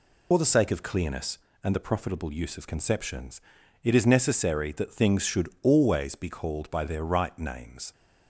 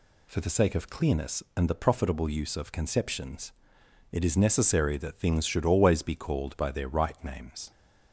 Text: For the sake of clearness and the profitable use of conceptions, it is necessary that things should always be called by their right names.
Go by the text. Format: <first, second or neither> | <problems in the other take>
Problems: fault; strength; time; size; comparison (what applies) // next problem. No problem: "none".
second | loses the start of "For"; at 0.3 s; 55 ms